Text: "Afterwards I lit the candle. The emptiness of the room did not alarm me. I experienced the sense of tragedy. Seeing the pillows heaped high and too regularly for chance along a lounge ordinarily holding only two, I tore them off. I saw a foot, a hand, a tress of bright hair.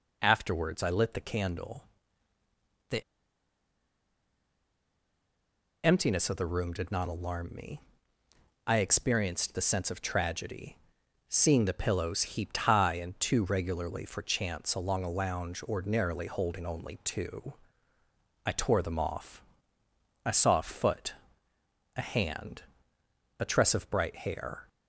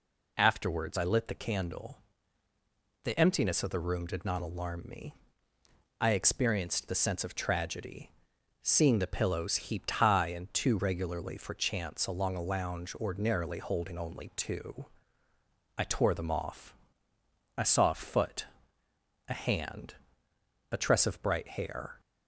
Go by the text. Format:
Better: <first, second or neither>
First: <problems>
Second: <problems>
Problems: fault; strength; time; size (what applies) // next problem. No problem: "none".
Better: second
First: pauses between "The" and "emptiness"; strong; at 3.0 s; 2.8 s long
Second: none